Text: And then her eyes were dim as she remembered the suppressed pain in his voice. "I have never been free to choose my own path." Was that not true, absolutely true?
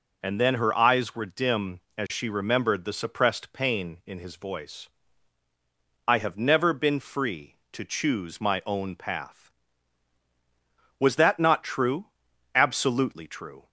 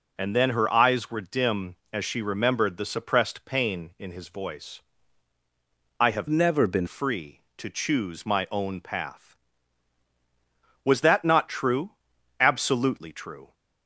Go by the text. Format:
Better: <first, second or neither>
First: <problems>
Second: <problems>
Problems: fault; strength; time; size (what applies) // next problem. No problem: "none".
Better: first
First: none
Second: changes voice from "never" to "been"; from 6.3 to 6.8 s; 0.5 s long